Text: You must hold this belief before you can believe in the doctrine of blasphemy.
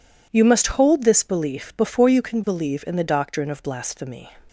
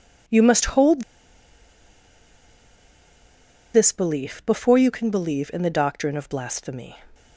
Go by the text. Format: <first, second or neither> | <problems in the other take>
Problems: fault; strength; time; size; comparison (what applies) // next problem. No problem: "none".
first | pauses between "hold" and "this"; strong; at 1.0 s; 2.7 s long